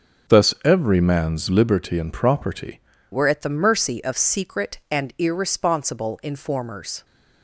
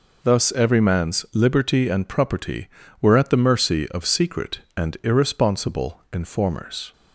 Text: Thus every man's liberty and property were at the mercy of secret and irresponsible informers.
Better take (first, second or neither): second